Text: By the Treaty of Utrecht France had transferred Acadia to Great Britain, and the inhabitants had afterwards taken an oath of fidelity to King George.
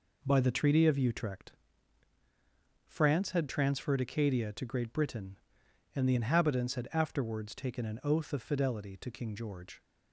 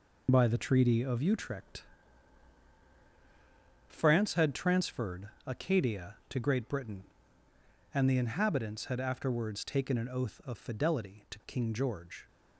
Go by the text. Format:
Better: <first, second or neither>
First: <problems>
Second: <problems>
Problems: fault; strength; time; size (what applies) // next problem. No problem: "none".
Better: first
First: pauses between "Utrecht" and "France"; strong; at 1.4 s; 1.3 s long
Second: loses the start of "By"; at 0.2 s; 50 ms // pauses between "Utrecht" and "France"; strong; at 1.8 s; 2.0 s long // pauses between "transferred" and "Acadia"; slight; at 5.2 s; 0.18 s long